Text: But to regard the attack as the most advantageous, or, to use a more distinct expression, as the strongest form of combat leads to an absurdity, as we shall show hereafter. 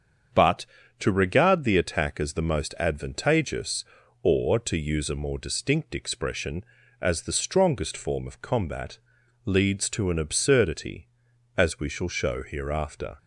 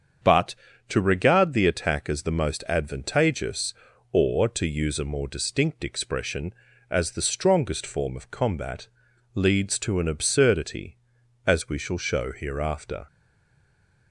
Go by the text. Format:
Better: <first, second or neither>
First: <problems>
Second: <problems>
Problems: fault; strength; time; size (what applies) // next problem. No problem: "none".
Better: first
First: starts louder than the rest; strong; until 1.6 s; 7.5 dB // pauses between "combat" and "leads"; noticeable; at 8.9 s; 0.46 s long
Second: starts louder than the rest; strong; until 1.5 s; 7.5 dB // pauses between "combat" and "leads"; noticeable; at 8.8 s; 0.46 s long // stays silent after the last word; from 13.0 s on; 1.1 s long